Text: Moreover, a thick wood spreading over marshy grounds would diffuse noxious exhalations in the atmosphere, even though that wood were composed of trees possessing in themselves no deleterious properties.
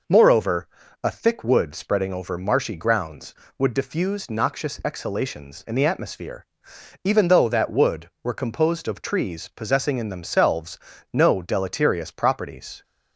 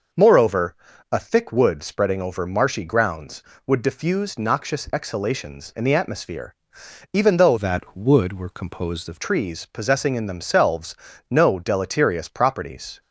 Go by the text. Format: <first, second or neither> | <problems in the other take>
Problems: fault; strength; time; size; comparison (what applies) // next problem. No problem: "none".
first | changes voice from "that" to "of"; from 7.5 to 9.1 s; 1.6 s long // pauses between "themselves" and "no"; slight; at 10.9 s; 0.36 s long; slight in the first